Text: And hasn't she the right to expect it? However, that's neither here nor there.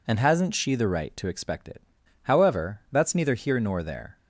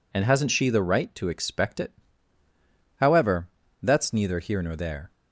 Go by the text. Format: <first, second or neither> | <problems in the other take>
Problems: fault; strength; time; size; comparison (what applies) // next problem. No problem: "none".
neither | none